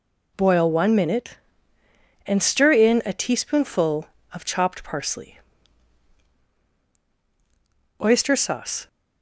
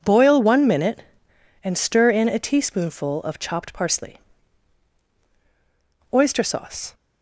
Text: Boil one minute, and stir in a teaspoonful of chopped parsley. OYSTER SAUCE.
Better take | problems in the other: neither | none

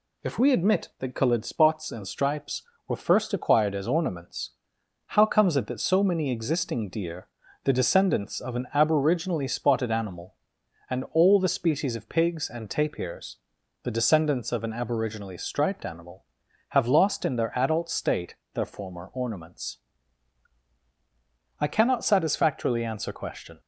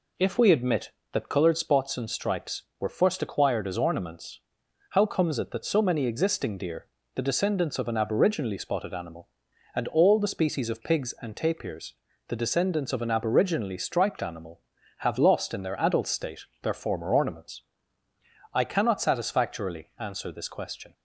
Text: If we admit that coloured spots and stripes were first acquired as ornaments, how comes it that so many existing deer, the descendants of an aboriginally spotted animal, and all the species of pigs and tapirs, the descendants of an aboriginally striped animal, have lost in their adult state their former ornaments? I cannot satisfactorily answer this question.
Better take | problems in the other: second | pauses between "state" and "their"; slight; at 18.3 s; 0.20 s long; slight in the second // skips "this"; at 23.1 s

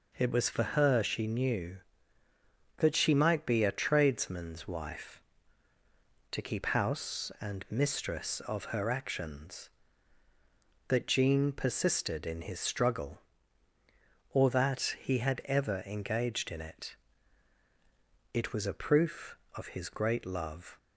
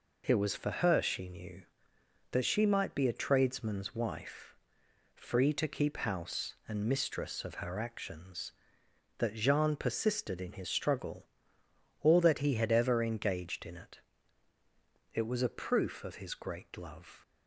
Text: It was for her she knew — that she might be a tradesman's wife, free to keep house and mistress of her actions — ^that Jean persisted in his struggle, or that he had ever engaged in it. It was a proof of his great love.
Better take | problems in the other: second | skips "free"; at 5.7 s

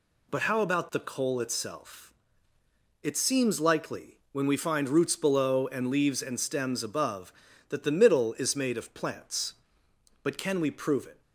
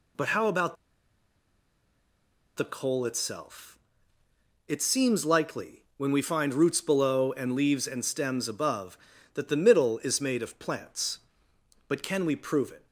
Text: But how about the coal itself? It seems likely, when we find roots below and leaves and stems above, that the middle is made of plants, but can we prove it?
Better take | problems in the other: first | pauses between "about" and "the"; strong; at 0.7 s; 1.8 s long

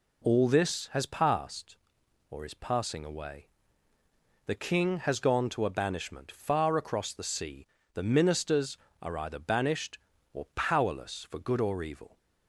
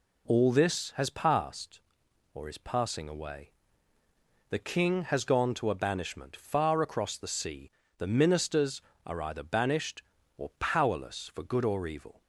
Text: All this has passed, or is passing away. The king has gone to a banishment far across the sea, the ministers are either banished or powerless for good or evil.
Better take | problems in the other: neither | none

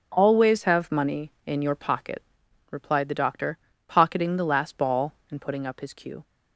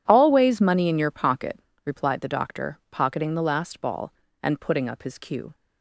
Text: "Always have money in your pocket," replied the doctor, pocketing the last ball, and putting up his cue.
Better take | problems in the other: first | skips "have"; at 0.6 s

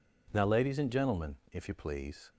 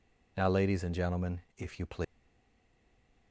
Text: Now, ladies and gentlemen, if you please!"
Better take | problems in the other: first | stays silent after the last word; noticeable; from 2.0 s on; 1.3 s long

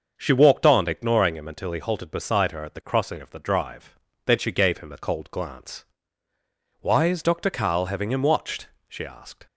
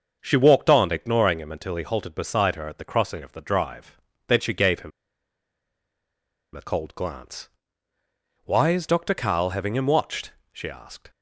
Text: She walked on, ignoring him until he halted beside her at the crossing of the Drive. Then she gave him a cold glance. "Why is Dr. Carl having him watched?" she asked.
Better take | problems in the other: first | starts louder than the rest; until 1.2 s; 6.5 dB; also in the first // pauses between "him" and "a"; strong; at 4.9 s; 1.6 s long

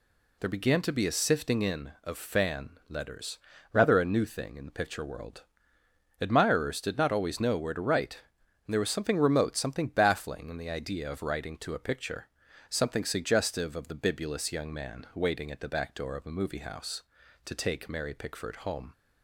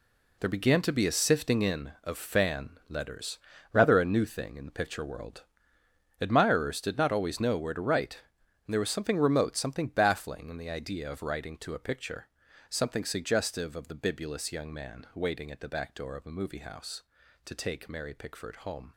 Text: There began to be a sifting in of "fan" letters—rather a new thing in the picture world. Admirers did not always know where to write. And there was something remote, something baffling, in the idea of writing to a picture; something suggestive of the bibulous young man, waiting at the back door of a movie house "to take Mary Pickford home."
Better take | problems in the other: first | gets quieter; strong; throughout; 10.5 dB

